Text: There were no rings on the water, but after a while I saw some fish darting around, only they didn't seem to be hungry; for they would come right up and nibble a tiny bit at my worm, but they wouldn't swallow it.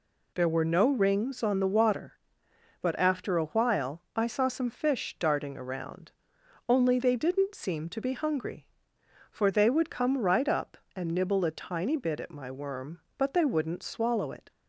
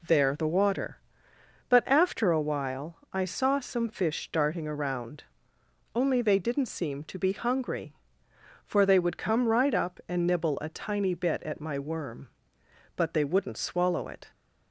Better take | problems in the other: first | skips "were no rings on"; at 0.3 s // pauses between "while" and "I"; slight; at 2.9 s; 0.16 s long

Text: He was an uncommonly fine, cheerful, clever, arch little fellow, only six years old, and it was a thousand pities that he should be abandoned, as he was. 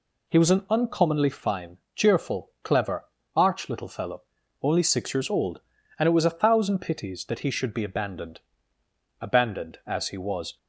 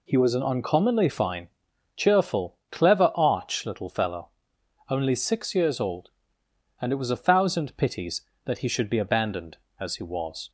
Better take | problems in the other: second | says "abandoned" twice; at 9.1 s

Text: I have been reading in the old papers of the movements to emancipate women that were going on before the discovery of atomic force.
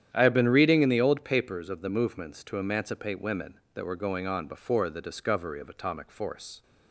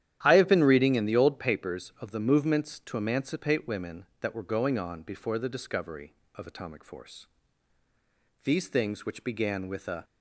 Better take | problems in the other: first | starts louder than the rest; strong; until 1.2 s; 11 dB; strong in the first // goes on to say "These things which began with a"; from 8.4 s on; 1.6 s long

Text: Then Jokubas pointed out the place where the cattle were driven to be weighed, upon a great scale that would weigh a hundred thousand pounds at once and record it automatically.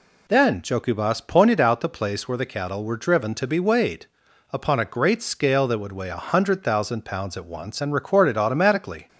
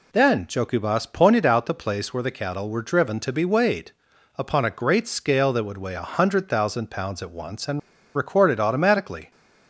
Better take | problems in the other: first | pauses between "and" and "record"; slight; at 7.7 s; 0.35 s long

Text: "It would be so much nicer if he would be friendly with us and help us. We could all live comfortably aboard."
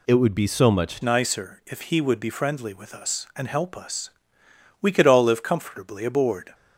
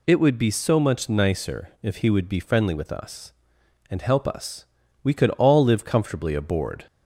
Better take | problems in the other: second | changes voice at "nicer"; from 1.0 s on; 5.5 s long

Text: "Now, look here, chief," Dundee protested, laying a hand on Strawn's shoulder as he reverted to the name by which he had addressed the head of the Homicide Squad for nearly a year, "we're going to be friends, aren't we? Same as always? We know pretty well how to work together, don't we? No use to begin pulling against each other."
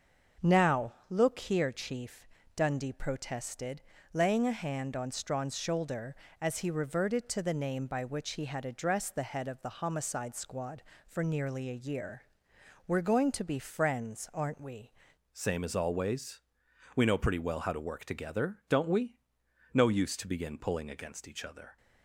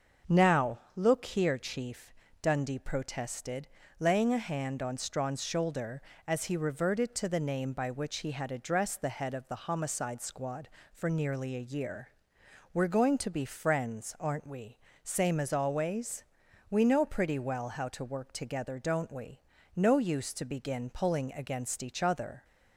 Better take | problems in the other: second | starts louder than the rest; until 1.5 s; 6.5 dB; also in the second // changes voice at "Same"; from 15.3 s on; 6.4 s long

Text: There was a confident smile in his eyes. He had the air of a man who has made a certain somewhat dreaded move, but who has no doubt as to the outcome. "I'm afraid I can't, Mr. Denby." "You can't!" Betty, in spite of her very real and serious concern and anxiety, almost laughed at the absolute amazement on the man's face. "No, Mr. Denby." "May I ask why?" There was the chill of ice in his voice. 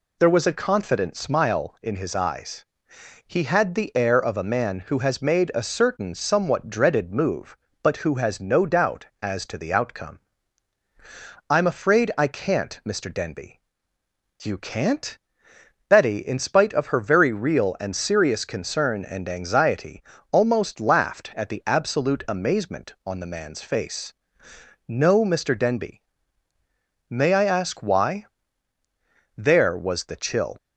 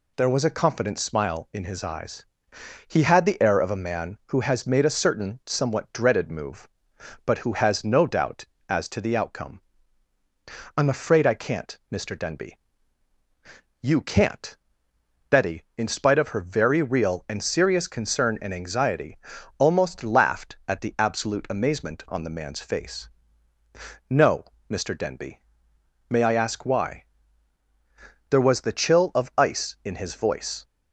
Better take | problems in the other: second | stops before "of ice in his voice"; at 30.5 s

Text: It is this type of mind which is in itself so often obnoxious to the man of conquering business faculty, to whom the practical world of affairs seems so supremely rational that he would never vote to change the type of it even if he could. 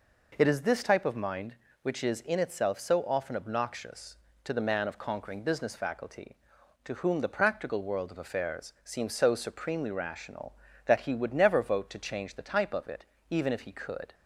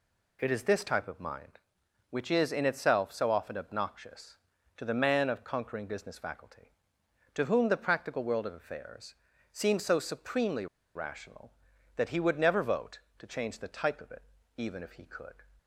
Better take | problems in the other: first | pauses between "affairs" and "seems"; at 9.1 s; 0.38 s long // pauses between "supremely" and "rational"; slight; at 10.6 s; 0.29 s long // pauses between "it" and "even"; slight; at 14.2 s; 0.34 s long; slight in the first

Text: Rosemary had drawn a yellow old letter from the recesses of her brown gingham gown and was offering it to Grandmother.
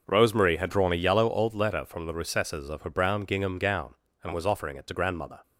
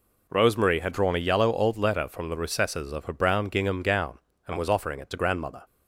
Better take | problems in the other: second | starts louder than the rest; noticeable; until 1.3 s; 6 dB

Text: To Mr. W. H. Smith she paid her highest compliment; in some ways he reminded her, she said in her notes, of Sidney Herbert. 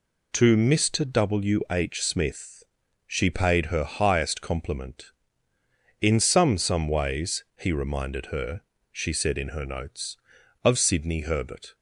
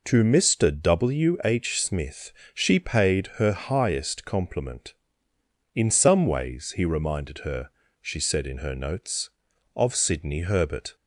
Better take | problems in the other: second | pauses between "Smith" and "she"; noticeable; at 2.6 s; 0.46 s long; slight in the second // says "some" twice; at 6.5 s

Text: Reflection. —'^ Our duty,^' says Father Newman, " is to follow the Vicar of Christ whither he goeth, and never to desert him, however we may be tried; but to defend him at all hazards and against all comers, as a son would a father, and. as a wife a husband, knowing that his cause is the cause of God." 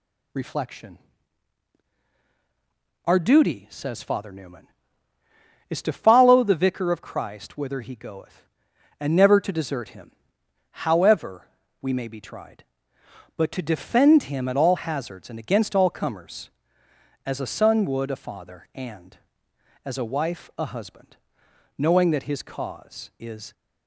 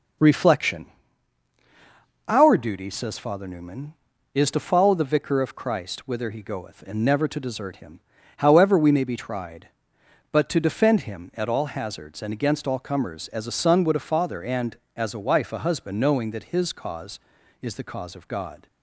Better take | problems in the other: second | pauses between "however" and "we"; slight; at 11.4 s; 0.34 s long // stops before "the cause of God"; at 23.5 s

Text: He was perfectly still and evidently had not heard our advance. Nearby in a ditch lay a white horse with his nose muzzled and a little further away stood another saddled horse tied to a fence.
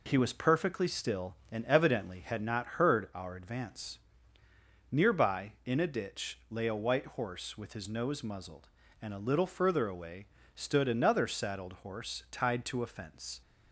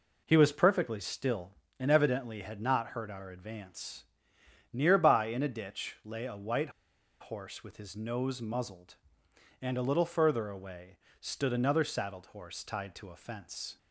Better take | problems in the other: first | pauses between "white" and "horse"; noticeable; at 6.6 s; 0.51 s long // pauses between "away" and "stood"; slight; at 10.9 s; 0.22 s long; slight in the first

